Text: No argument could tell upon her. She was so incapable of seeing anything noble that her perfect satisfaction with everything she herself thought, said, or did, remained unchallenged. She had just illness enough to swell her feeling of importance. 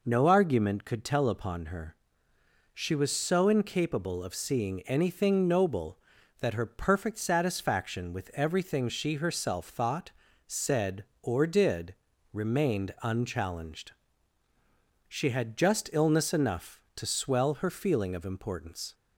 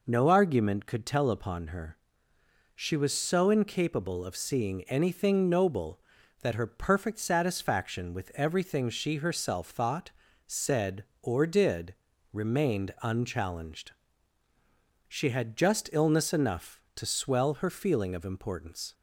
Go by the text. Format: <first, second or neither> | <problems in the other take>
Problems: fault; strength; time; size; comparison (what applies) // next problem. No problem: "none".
neither | none